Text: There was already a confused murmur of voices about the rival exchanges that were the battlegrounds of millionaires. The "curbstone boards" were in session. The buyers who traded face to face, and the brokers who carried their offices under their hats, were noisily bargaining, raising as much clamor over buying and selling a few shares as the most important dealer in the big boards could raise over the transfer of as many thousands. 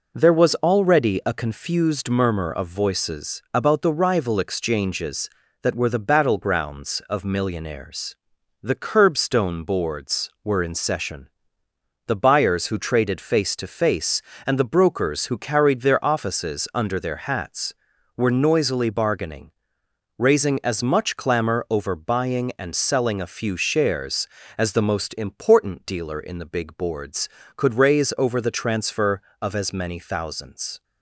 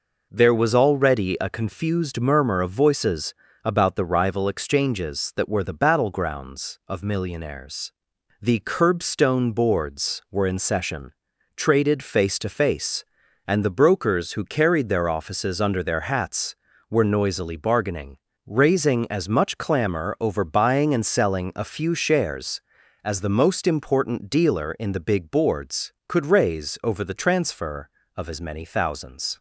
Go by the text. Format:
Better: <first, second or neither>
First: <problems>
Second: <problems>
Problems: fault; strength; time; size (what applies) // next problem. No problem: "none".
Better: first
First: none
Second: pauses between "voices" and "about"; slight; at 3.3 s; 0.28 s long // skips "The buyers who"; at 11.3 s